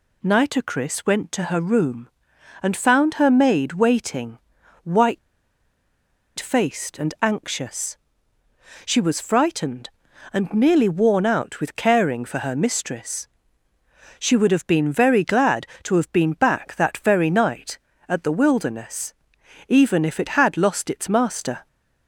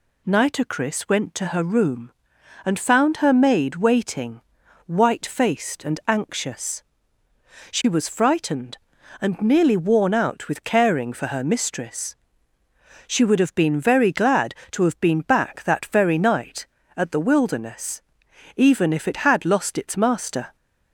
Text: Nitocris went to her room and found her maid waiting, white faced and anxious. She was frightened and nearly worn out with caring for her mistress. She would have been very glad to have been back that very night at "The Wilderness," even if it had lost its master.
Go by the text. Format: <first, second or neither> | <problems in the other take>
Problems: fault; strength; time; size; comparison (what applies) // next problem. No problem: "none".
second | pauses between "white" and "faced"; at 5.1 s; 1.1 s long